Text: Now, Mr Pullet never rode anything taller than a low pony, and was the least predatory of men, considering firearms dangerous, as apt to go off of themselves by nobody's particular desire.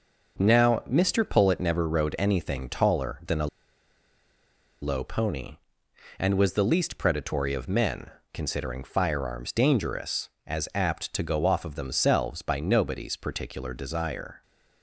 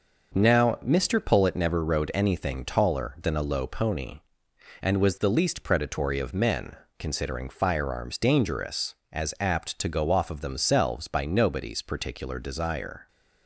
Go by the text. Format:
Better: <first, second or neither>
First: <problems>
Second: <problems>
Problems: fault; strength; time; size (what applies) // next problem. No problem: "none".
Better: second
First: pauses between "a" and "low"; strong; at 3.4 s; 1.3 s long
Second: none